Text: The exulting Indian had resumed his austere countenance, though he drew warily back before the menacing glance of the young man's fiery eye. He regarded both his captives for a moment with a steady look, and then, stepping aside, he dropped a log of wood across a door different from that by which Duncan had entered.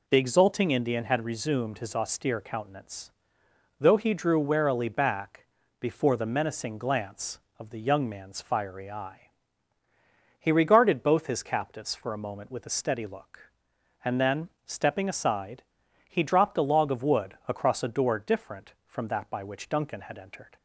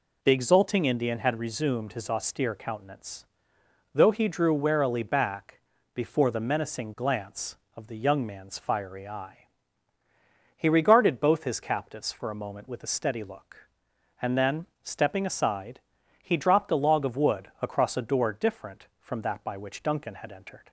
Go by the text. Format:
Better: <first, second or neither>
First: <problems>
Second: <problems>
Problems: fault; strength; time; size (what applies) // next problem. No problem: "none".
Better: neither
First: pauses between "back" and "before"; slight; at 5.4 s; 0.34 s long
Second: pauses between "back" and "before"; slight; at 5.6 s; 0.34 s long